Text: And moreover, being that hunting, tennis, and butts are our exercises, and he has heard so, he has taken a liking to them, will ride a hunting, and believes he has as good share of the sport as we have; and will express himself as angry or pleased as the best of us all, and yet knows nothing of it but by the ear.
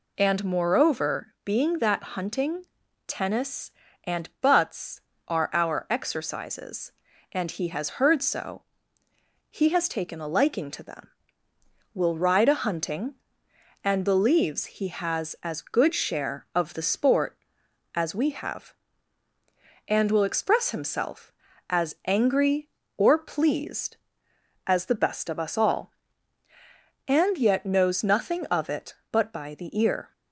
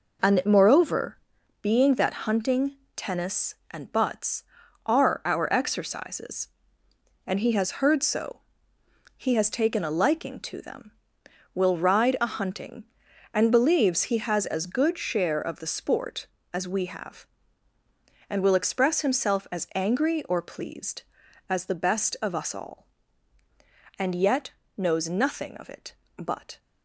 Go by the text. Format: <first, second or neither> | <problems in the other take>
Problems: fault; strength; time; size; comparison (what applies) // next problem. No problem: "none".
first | pauses between "yet" and "knows"; slight; at 24.5 s; 0.26 s long // stops before "by the ear"; at 26.5 s